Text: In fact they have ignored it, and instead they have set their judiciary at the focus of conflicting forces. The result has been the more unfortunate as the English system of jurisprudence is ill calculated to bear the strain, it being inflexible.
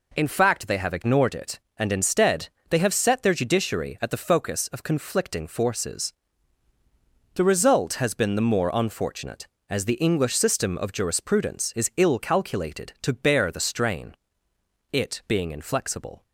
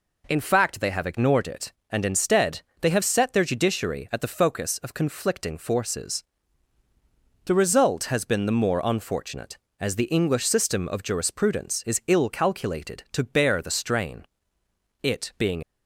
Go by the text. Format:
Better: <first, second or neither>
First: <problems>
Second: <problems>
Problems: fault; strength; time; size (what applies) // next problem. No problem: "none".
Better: first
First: pauses between "instead" and "they"; slight; at 2.4 s; 0.21 s long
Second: pauses between "instead" and "they"; slight; at 2.6 s; 0.20 s long // stops before "inflexible"; at 15.6 s